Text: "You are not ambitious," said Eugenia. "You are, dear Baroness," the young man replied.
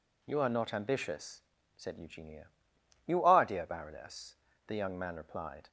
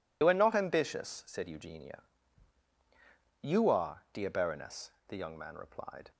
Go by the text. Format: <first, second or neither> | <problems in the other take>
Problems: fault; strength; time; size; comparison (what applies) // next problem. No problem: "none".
first | loses the start of "You"; at 0.2 s; 50 ms